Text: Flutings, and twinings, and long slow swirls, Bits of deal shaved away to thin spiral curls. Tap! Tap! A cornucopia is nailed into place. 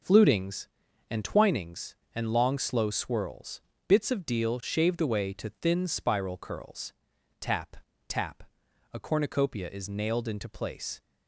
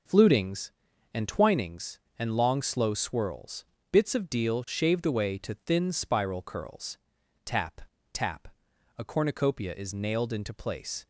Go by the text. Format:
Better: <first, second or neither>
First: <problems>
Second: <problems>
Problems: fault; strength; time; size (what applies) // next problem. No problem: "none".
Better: neither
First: none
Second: none